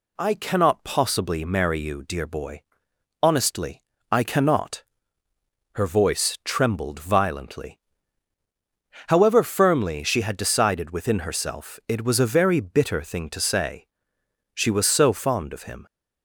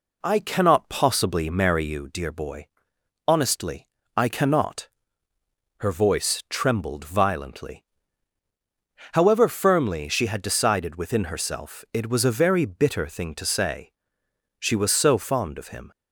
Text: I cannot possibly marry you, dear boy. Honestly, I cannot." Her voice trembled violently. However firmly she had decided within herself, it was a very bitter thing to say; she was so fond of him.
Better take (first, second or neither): first